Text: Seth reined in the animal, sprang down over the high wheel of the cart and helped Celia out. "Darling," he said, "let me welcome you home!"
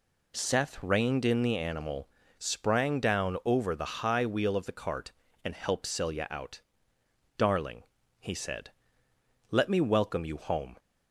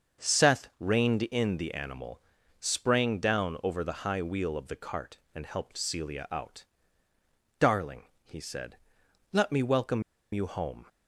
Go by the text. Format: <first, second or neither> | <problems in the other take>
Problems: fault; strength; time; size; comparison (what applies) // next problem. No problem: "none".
first | starts louder than the rest; until 1.3 s; 6.5 dB // pauses between "welcome" and "you"; slight; at 10.0 s; 0.30 s long